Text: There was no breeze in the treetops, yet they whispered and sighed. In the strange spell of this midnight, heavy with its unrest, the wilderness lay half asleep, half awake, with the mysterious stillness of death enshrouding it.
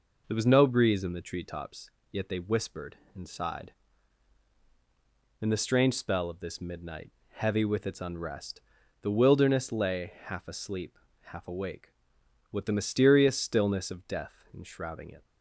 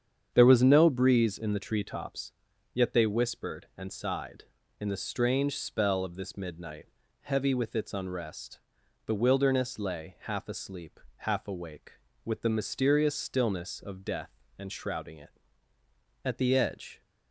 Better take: first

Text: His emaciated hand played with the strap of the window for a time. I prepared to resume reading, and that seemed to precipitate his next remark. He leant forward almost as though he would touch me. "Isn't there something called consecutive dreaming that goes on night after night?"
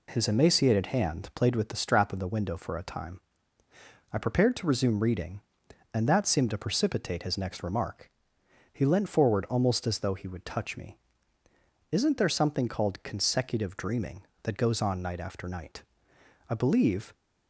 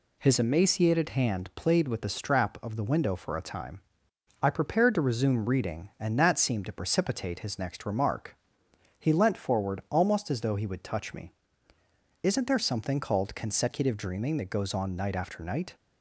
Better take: second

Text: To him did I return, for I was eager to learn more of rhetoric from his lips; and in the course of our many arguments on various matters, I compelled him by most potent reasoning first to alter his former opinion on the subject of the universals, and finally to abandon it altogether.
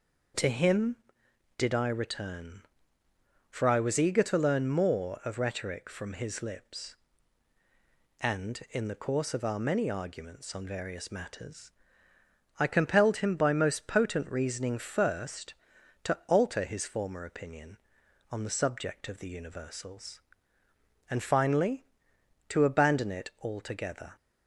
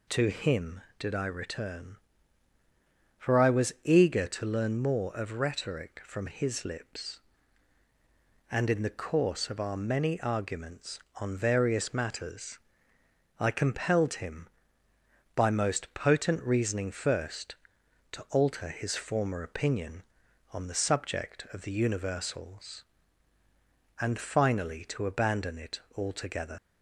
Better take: first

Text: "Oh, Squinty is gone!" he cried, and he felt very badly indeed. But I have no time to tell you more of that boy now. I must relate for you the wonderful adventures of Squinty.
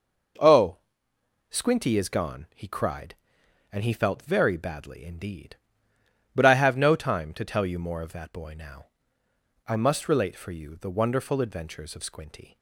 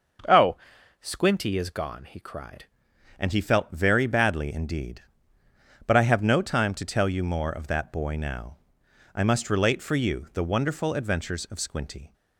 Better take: first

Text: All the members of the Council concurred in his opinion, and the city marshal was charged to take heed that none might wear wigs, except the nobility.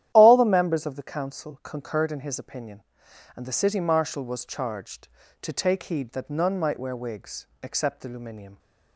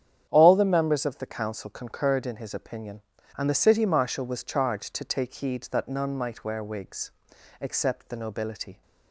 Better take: second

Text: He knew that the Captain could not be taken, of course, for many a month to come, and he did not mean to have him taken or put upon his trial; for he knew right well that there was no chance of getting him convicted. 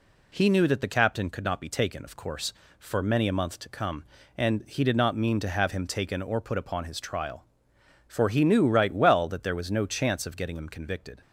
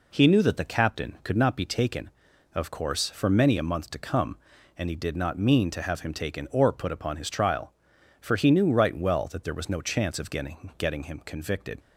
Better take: first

